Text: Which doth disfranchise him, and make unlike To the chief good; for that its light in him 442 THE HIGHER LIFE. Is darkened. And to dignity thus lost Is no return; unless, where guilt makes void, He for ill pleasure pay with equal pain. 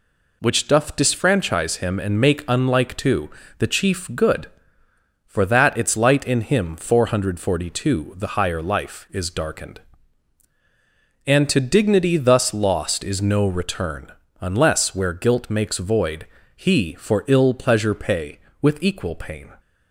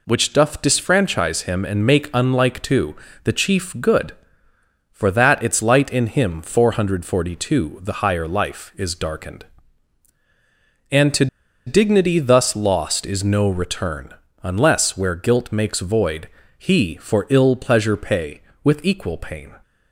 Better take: first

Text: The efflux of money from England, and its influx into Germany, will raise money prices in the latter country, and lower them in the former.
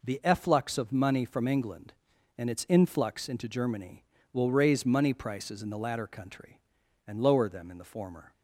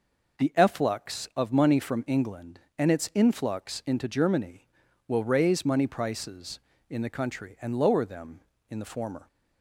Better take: first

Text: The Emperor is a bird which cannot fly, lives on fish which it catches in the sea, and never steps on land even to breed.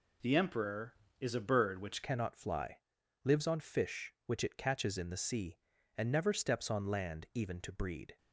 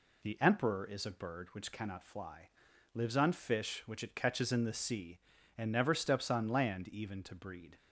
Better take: second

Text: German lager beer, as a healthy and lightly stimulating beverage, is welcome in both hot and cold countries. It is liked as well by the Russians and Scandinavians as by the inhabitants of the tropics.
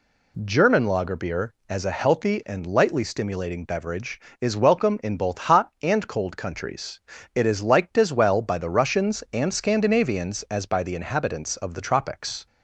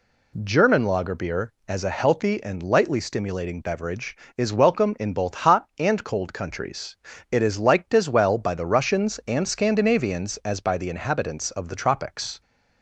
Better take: neither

